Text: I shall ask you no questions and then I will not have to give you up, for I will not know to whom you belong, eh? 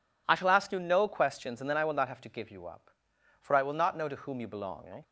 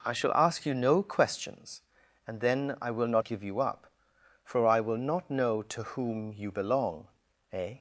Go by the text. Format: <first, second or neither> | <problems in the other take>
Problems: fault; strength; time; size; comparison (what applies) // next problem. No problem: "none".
first | skips "have to"; at 3.2 s